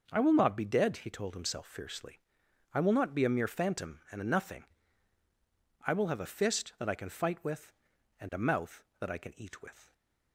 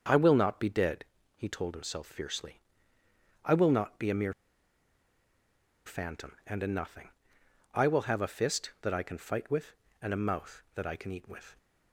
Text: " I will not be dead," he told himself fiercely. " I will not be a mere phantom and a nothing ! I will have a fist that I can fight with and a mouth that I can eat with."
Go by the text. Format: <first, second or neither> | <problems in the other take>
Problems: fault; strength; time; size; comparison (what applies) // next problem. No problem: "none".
first | starts louder than the rest; until 1.3 s; 7 dB // pauses between "mere" and "phantom"; strong; at 4.3 s; 1.5 s long